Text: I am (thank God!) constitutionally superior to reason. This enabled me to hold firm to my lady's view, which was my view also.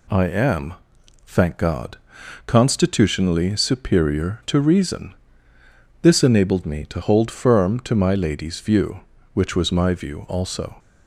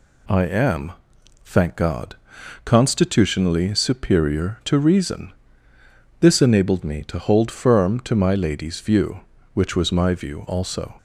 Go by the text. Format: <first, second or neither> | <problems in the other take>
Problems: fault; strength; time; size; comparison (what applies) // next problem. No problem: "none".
neither | none